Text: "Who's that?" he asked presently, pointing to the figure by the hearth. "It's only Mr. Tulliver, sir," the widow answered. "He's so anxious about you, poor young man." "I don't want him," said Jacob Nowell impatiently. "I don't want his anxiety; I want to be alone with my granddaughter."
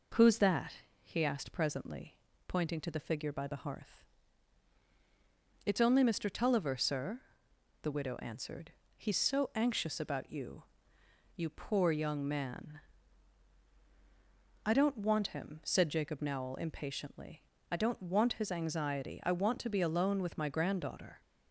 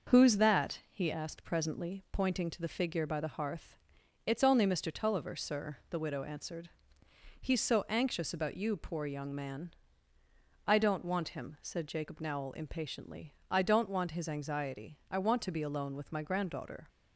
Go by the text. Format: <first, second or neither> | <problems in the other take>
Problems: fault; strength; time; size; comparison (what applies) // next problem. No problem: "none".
second | says "you" twice; at 11.3 s